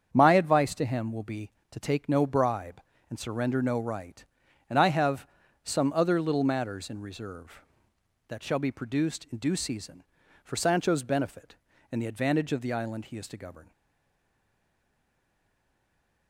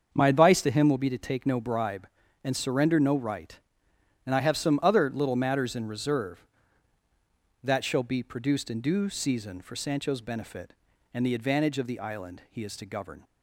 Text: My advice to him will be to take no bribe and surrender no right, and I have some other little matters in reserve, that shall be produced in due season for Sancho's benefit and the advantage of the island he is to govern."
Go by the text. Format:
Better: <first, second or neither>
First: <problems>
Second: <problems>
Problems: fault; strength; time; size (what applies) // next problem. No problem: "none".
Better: second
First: starts louder than the rest; strong; until 1.1 s; 7.5 dB // pauses between "have" and "some"; at 5.2 s; 0.38 s long // stays silent after the last word; strong; from 13.7 s on; 2.5 s long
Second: starts louder than the rest; until 1.1 s; 7 dB